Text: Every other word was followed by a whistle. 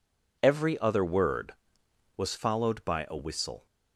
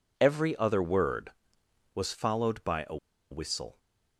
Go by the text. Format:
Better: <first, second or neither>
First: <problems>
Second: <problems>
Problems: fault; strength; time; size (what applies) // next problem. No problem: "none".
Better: first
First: none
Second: pauses between "a" and "whistle"; slight; at 2.9 s; 0.34 s long